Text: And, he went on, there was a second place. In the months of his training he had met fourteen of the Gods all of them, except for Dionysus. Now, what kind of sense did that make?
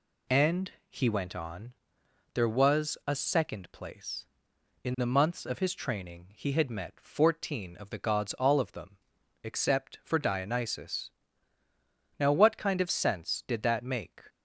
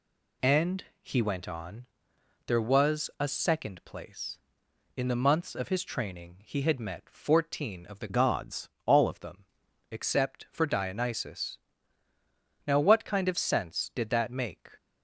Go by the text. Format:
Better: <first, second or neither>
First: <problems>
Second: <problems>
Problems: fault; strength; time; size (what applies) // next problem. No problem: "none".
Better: first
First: none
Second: changes voice from "Gods" to "all"; from 8.0 to 9.0 s; 1.0 s long // pauses between "Gods" and "all"; slight; at 8.6 s; 0.16 s long